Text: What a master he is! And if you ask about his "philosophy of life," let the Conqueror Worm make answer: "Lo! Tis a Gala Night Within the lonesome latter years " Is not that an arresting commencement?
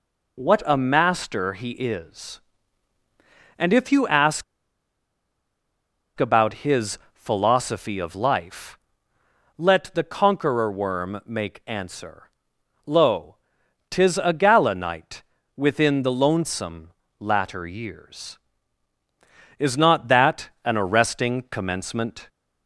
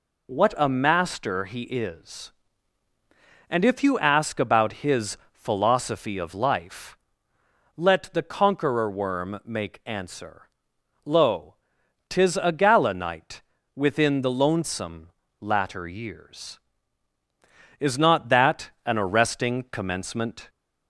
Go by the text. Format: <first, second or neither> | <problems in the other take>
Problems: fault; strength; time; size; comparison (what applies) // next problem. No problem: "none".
second | pauses between "ask" and "about"; strong; at 4.4 s; 1.7 s long // pauses between "his" and "philosophy"; slight; at 6.9 s; 0.16 s long; slight in the second // pauses between "Night" and "Within"; slight; at 15.2 s; 0.32 s long; slight in the second // pauses between "lonesome" and "latter"; slight; at 16.8 s; 0.32 s long; slight in the second // pauses between "that" and "an"; slight; at 20.4 s; 0.16 s long; slight in the second